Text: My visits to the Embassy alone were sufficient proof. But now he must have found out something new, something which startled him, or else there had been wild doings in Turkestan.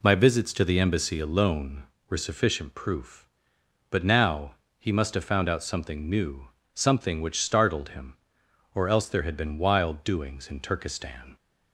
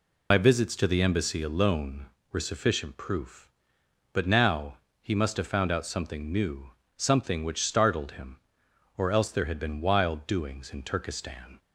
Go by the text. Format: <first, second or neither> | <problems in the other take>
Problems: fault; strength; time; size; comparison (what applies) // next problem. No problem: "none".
first | loses the start of "My"; at 0.3 s; 50 ms // pauses between "now" and "he"; slight; at 4.7 s; 0.24 s long; slight in the first